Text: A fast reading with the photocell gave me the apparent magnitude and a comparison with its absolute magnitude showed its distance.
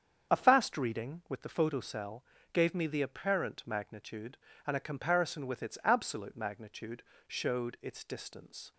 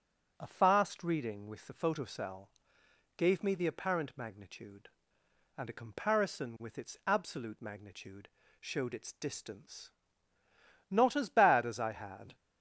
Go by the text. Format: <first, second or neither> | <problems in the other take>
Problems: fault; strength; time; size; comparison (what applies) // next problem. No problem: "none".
first | starts louder than the rest; until 1.3 s; 6.5 dB; strong in the first // pauses between "photocell" and "gave"; noticeable; at 2.4 s; 0.66 s long; slight in the first // pauses between "magnitude" and "showed"; slight; at 8.2 s; 0.32 s long; slight in the first // goes on to say "Not as bad as I had"; from 10.8 s on; 1.4 s long